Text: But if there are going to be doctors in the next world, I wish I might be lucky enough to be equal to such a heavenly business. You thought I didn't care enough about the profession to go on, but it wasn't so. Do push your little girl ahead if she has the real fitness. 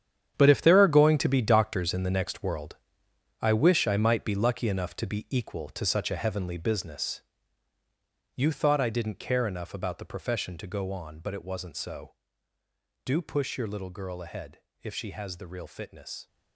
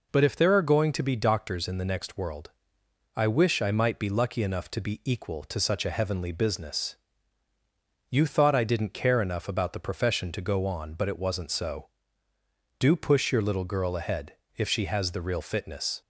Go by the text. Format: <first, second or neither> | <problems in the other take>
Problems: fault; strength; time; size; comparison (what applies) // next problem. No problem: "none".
second | gets quieter; strong; throughout; 12 dB // pauses between "ahead" and "if"; slight; at 14.5 s; 0.24 s long; slight in the second